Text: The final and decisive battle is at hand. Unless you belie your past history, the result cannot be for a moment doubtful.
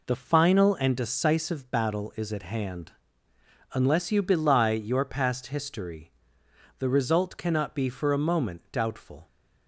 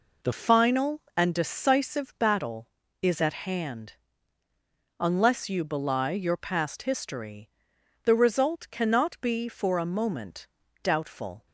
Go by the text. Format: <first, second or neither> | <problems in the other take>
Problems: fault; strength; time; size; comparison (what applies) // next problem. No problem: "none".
first | changes voice at "final"; from 0.3 s on; 11.1 s long // pauses between "moment" and "doubtful"; slight; at 10.4 s; 0.36 s long